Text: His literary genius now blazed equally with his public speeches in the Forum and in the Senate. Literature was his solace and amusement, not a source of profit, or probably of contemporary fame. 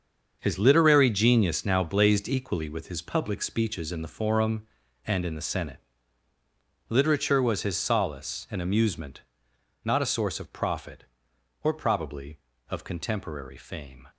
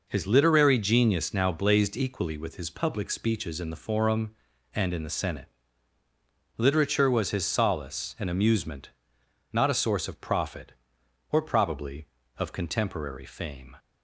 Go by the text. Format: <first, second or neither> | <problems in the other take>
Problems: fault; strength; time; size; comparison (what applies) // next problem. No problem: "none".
second | gets quieter; strong; throughout; 10 dB